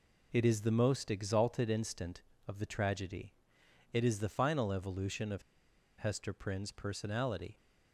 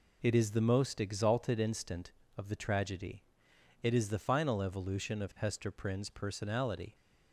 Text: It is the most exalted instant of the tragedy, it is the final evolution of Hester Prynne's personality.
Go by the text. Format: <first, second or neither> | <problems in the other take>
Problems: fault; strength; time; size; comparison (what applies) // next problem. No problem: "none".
second | pauses between "of" and "Hester"; noticeable; at 5.4 s; 0.56 s long